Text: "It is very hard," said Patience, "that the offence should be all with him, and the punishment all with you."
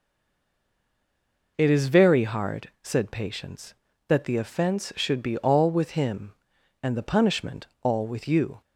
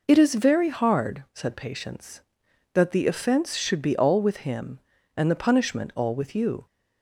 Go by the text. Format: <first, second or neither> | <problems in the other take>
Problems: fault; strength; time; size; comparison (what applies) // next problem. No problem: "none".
second | stays silent before the first word; noticeable; until 1.5 s; 1.5 s long